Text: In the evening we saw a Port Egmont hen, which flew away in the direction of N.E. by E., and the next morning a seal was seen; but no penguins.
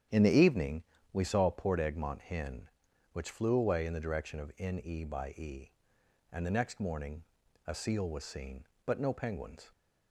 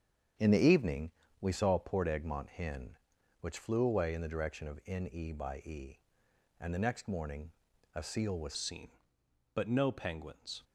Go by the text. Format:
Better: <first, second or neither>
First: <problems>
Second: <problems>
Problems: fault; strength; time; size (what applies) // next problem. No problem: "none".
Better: first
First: starts louder than the rest; strong; until 1.3 s; 9 dB // pauses between "evening" and "we"; slight; at 0.8 s; 0.28 s long // pauses between "morning" and "a"; at 7.2 s; 0.42 s long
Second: starts louder than the rest; strong; until 1.6 s; 8 dB // pauses between "evening" and "we"; slight; at 1.1 s; 0.28 s long // pauses between "morning" and "a"; at 7.5 s; 0.42 s long // changes voice at "seen"; from 8.5 s on; 2.1 s long